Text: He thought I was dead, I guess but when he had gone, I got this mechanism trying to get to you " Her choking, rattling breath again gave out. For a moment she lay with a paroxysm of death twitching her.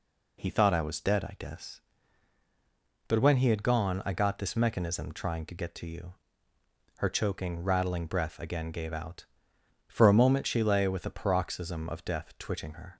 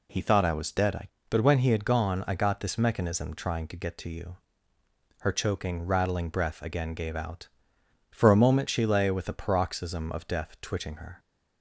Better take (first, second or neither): first